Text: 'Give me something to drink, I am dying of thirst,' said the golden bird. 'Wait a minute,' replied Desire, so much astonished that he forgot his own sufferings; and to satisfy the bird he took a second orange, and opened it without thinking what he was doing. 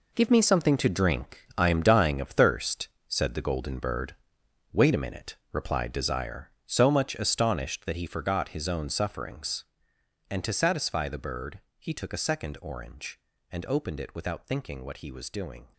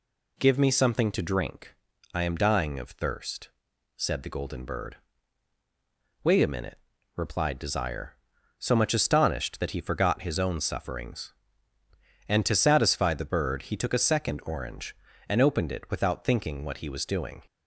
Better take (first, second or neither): second